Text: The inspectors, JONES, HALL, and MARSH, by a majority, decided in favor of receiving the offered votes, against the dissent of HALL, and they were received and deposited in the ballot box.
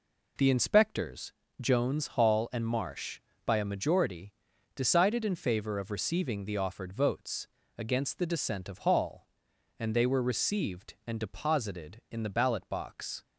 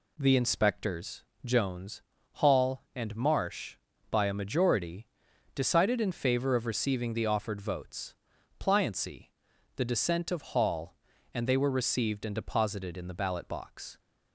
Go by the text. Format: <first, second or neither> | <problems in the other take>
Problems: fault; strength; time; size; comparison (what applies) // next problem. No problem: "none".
first | says "pliancy" for "against"; at 8.5 s